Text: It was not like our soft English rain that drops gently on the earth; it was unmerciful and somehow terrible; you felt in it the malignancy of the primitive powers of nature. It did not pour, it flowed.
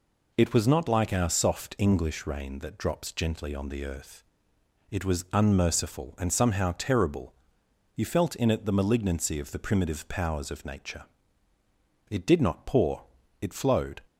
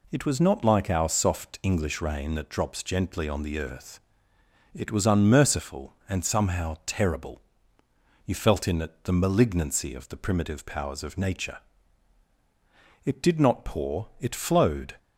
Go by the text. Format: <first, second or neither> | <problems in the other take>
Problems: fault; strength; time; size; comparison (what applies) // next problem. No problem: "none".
neither | none